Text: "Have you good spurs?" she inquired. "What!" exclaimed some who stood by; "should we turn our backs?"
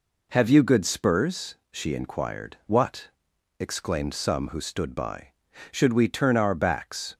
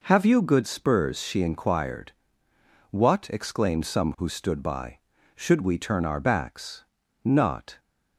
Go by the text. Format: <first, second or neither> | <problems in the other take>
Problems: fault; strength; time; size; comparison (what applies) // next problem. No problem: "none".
first | goes on to say "Not"; from 7.2 s on; 0.56 s long